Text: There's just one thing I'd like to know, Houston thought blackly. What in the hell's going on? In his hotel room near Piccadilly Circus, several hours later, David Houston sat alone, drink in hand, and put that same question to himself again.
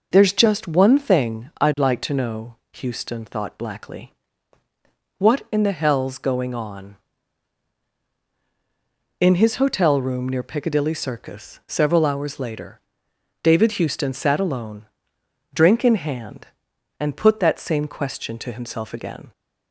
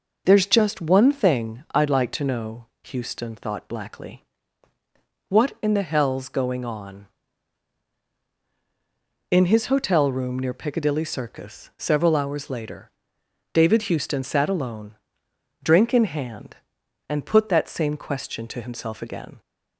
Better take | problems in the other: neither | none

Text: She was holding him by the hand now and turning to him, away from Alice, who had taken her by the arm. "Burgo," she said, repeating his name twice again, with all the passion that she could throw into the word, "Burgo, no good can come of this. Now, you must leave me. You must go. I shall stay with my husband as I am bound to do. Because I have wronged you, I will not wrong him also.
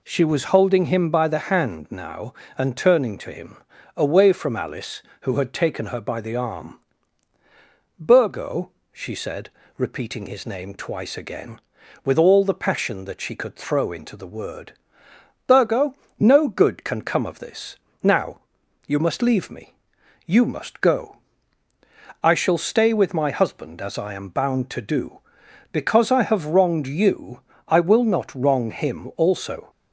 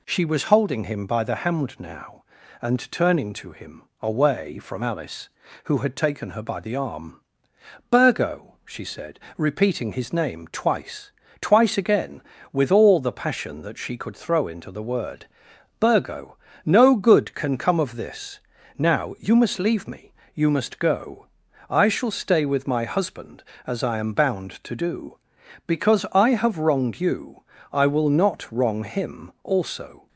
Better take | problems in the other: first | says "twice" twice; at 11.4 s

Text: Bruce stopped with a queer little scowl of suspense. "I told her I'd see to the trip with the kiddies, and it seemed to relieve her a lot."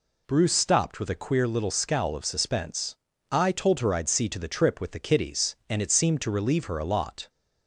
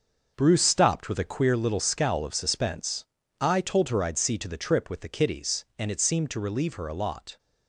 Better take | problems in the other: first | gets quieter; strong; throughout; 9 dB

